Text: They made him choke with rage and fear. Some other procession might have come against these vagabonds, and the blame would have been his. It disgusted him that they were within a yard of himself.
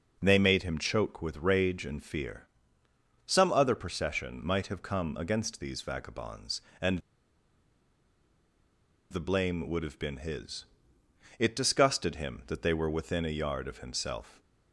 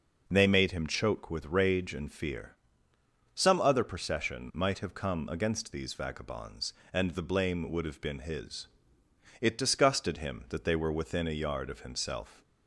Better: second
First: pauses between "and" and "the"; strong; at 7.0 s; 2.1 s long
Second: none

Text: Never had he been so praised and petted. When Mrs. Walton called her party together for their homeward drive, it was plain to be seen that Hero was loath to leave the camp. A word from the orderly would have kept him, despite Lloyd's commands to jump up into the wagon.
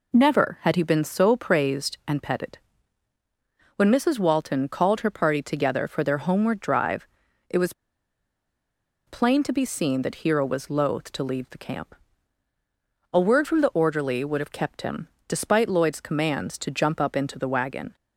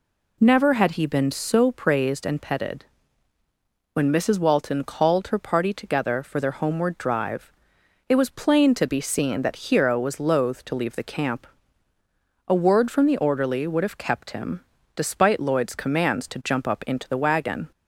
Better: second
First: pauses between "was" and "plain"; strong; at 7.7 s; 1.3 s long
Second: none

